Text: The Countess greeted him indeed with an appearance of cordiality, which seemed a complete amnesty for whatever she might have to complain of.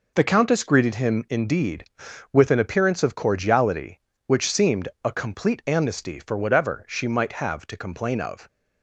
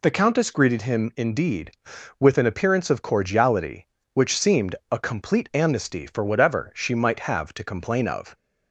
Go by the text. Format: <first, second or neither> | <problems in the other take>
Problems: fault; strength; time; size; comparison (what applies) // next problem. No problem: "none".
second | gets quieter; strong; throughout; 7 dB // pauses between "seemed" and "a"; slight; at 4.8 s; 0.16 s long; slight in the second